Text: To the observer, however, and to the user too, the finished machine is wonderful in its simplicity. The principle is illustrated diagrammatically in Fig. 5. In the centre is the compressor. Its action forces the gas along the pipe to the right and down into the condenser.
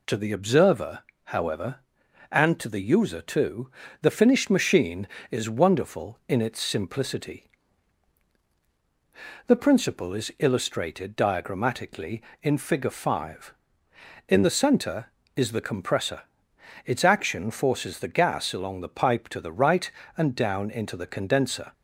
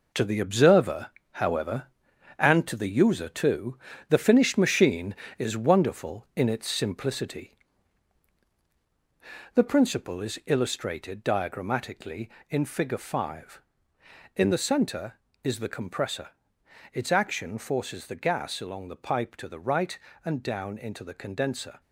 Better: first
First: none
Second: gets quieter; strong; throughout; 7.5 dB

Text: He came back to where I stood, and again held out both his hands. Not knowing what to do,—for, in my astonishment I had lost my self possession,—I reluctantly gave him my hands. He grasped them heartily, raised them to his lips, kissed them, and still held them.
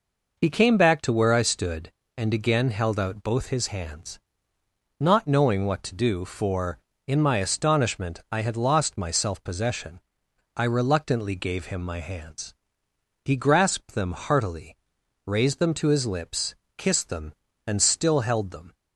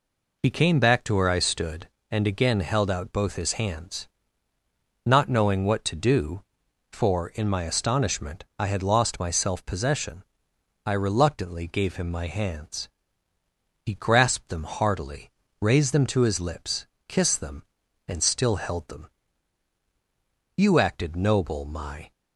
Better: first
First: none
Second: goes on to say "You acted noble my"; from 20.5 s on; 1.5 s long

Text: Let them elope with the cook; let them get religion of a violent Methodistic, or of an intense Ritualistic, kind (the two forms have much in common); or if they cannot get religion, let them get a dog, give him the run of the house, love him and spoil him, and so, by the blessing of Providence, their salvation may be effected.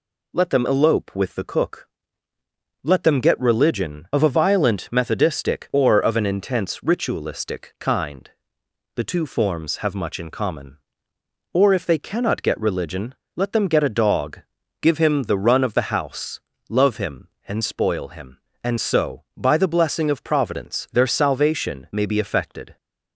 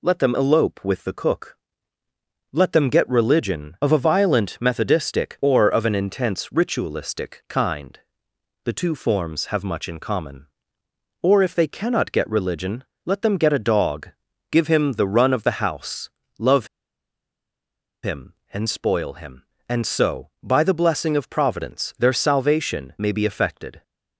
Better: first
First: none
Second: pauses between "love" and "him"; strong; at 16.6 s; 1.3 s long

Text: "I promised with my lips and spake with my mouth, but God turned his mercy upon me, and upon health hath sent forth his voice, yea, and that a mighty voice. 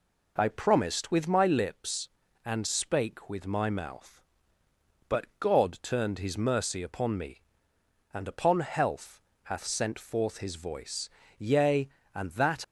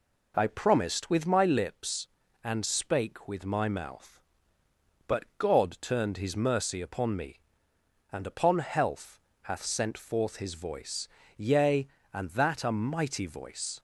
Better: second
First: pauses between "health" and "hath"; slight; at 9.2 s; 0.22 s long // stops before "a mighty voice"; at 12.6 s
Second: pauses between "health" and "hath"; slight; at 9.2 s; 0.22 s long

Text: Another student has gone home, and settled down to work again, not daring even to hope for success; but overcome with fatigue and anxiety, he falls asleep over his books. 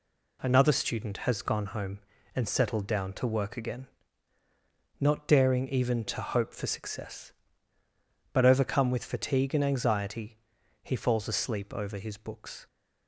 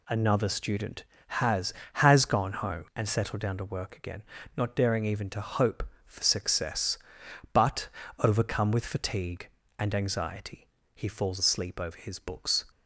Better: first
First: none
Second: says "has" twice; at 1.9 s // pauses between "but" and "overcome"; slight; at 7.8 s; 0.32 s long

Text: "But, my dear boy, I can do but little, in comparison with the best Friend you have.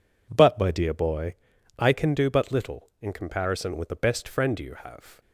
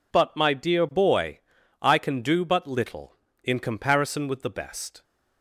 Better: first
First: none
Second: stops before "Friend you have"; at 5.0 s

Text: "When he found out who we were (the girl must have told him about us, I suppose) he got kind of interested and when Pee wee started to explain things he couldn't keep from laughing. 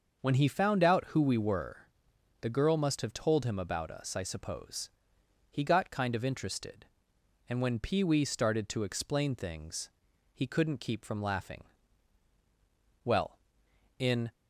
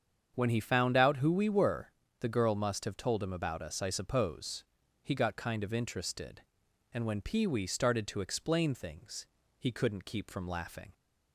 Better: second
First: starts louder than the rest; until 1.2 s; 6.5 dB // pauses between "things" and "he"; at 9.9 s; 0.42 s long // goes on to say "Well in"; noticeable; from 13.0 s on; 1.2 s long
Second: starts louder than the rest; strong; until 1.3 s; 7.5 dB // pauses between "things" and "he"; slight; at 9.2 s; 0.32 s long

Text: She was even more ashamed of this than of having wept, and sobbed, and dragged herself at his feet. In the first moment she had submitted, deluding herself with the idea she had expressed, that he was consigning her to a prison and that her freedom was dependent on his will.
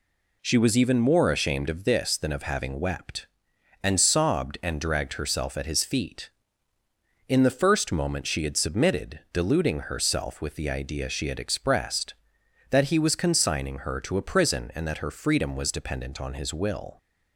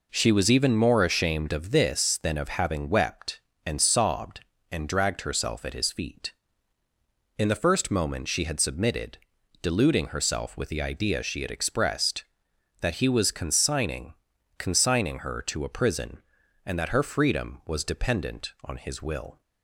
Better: first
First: none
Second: says "consigning" twice; at 14.5 s

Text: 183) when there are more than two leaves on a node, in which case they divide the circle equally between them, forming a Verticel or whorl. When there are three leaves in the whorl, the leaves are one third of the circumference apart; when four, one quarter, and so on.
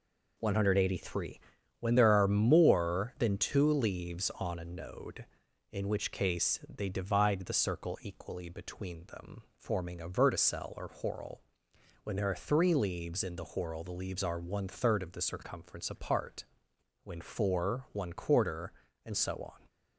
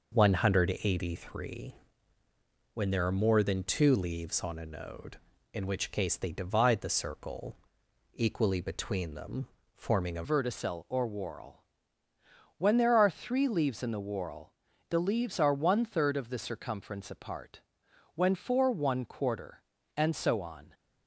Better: first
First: none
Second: pauses between "circle" and "equally"; noticeable; at 7.5 s; 0.56 s long // changes voice at "Verticel"; from 10.2 s on; 10.5 s long

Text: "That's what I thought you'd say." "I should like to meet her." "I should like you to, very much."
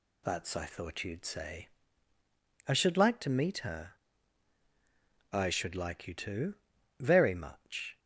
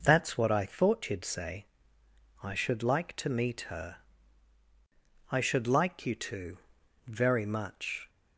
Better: second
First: skips "what"; at 0.5 s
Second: none

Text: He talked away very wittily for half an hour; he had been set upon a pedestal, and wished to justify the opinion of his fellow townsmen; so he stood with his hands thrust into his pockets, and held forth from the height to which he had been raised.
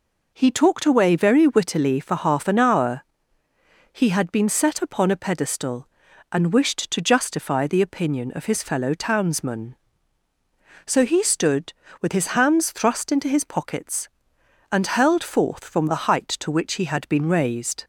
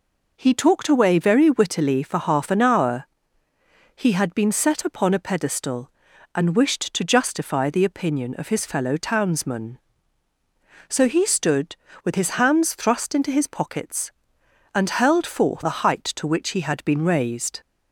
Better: first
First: none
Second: skips "from"; at 15.6 s

